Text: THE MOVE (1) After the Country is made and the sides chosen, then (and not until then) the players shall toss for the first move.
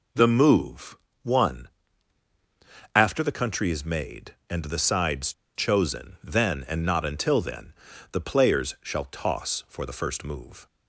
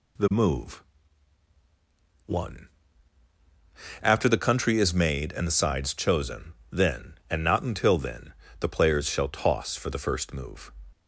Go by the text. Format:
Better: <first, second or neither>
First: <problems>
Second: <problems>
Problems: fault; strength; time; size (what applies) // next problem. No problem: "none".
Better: second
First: pauses between "sides" and "chosen"; slight; at 5.3 s; 0.23 s long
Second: none